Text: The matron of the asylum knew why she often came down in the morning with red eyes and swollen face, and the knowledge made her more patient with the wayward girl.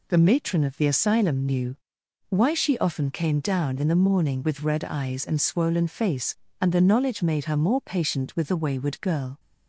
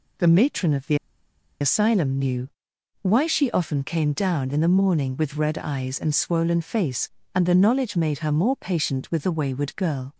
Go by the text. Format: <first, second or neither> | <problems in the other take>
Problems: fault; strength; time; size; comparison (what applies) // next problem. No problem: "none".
first | pauses between "the" and "asylum"; noticeable; at 0.9 s; 0.64 s long // pauses between "knew" and "why"; noticeable; at 2.4 s; 0.52 s long; noticeable in the first